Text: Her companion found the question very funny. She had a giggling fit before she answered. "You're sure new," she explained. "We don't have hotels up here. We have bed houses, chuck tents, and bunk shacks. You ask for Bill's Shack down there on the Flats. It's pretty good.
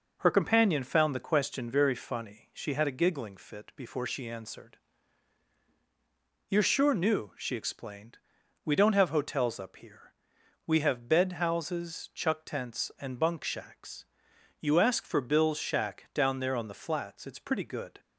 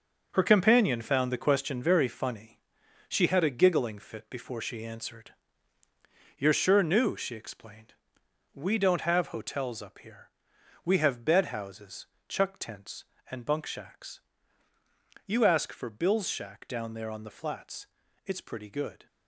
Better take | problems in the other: first | gets quieter; strong; throughout; 9 dB

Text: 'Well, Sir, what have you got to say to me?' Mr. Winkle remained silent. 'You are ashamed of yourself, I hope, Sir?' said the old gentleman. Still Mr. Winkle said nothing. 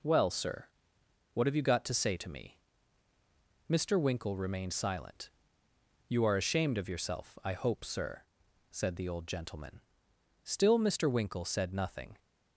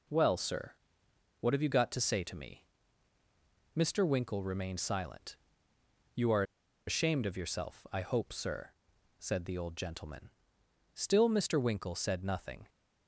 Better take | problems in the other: first | pauses between "are" and "ashamed"; at 6.4 s; 0.44 s long

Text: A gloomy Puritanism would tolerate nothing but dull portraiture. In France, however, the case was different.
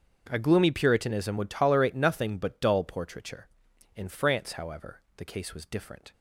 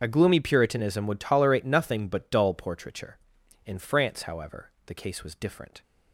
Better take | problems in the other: first | loses the start of "A"; at 0.0 s; 60 ms // starts louder than the rest; until 1.0 s; 7 dB; also in the first

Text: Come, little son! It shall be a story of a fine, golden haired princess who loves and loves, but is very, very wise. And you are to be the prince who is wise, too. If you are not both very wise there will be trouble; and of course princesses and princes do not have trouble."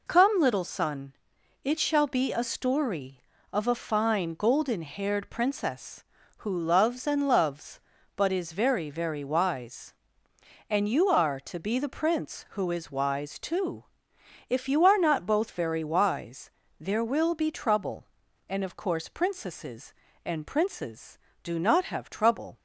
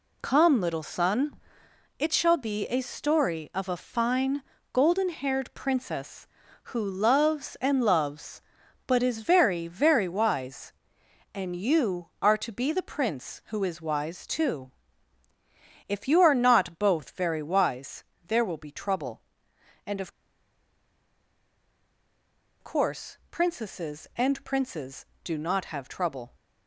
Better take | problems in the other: first | pauses between "wise" and "there"; slight; at 18.0 s; 0.24 s long; slight in the first // pauses between "of" and "course"; strong; at 20.1 s; 2.5 s long

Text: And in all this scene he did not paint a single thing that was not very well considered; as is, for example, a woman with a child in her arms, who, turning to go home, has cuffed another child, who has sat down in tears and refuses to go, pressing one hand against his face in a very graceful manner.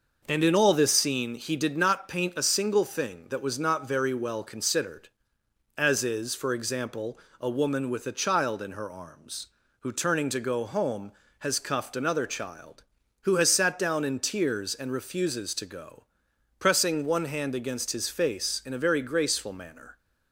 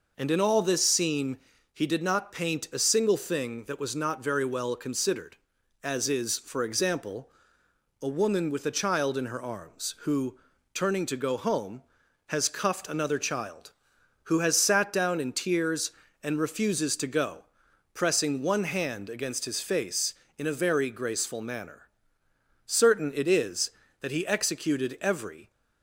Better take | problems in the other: first | pauses between "scene" and "he"; slight; at 1.3 s; 0.34 s long // goes on to say "Certain it is that he executed every"; strong; from 22.6 s on; 2.8 s long

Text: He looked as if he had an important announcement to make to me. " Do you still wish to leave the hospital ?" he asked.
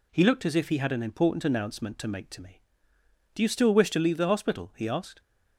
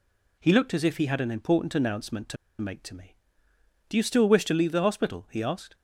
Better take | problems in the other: first | pauses between "to" and "make"; slight; at 2.3 s; 0.24 s long

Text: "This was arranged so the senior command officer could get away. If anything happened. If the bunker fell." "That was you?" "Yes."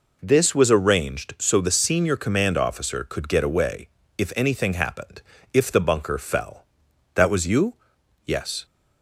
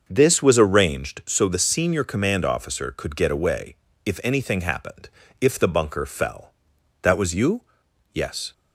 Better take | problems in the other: first | starts louder than the rest; until 1.1 s; 6.5 dB

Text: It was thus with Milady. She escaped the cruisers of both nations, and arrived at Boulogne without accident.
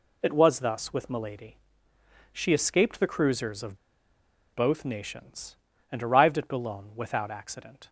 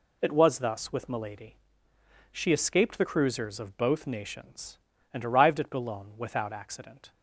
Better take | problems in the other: second | pauses between "of" and "both"; noticeable; at 3.7 s; 0.76 s long

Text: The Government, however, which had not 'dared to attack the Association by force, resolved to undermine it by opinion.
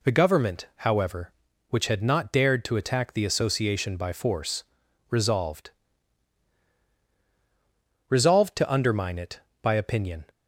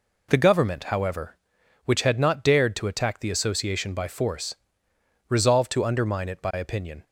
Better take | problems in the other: second | says "resolved" twice; at 8.0 s

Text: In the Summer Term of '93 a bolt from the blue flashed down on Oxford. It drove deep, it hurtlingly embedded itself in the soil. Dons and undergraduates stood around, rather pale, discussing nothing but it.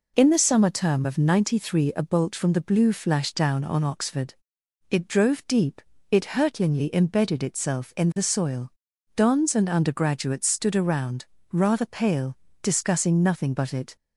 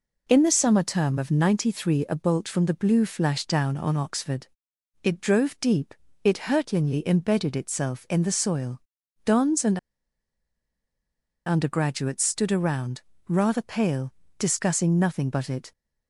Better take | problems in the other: first | pauses between "and" and "undergraduates"; strong; at 9.7 s; 1.6 s long

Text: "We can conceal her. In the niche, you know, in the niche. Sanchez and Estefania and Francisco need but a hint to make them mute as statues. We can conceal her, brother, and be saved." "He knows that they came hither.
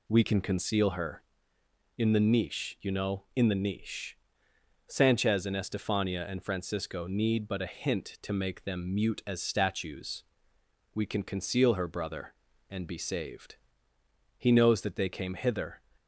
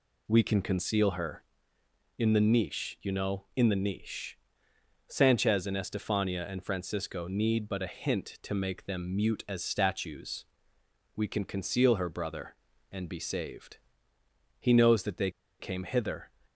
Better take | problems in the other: first | pauses between "they" and "came"; slight; at 15.2 s; 0.30 s long

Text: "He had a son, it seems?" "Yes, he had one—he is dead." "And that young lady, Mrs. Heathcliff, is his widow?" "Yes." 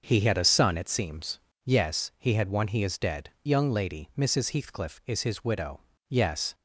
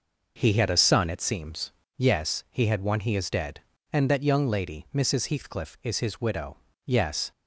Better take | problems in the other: second | starts louder than the rest; until 1.0 s; 6.5 dB // skips "And that"; at 3.3 s

